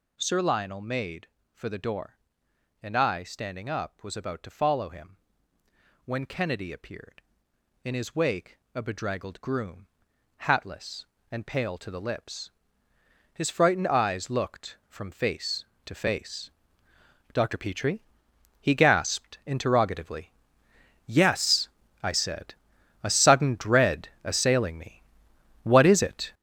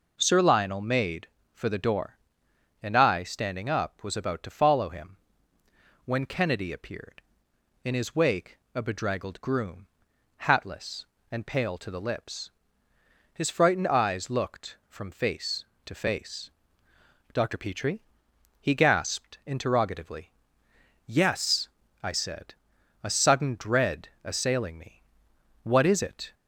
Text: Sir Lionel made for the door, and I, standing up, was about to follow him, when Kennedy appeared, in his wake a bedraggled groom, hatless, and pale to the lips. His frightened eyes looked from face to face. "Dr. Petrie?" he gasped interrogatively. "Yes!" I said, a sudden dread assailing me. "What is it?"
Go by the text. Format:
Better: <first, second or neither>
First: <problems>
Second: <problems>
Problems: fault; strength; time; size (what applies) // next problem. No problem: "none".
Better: second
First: gets louder; strong; throughout; 8.5 dB // pauses between "wake" and "a"; slight; at 8.5 s; 0.18 s long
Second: pauses between "wake" and "a"; slight; at 8.5 s; 0.18 s long